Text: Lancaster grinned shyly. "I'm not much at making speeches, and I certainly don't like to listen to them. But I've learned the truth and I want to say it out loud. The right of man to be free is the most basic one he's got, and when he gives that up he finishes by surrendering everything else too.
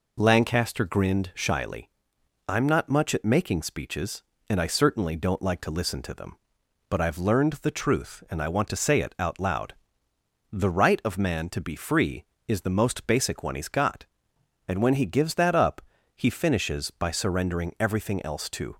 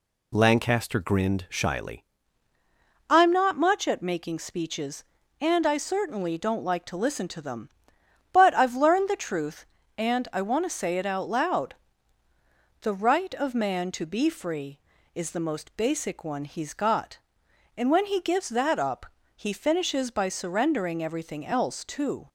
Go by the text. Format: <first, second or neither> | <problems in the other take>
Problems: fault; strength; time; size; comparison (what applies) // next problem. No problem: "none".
first | changes voice at "I'm"; from 3.0 s on; 19.2 s long // pauses between "up" and "he"; slight; at 19.0 s; 0.28 s long; slight in the first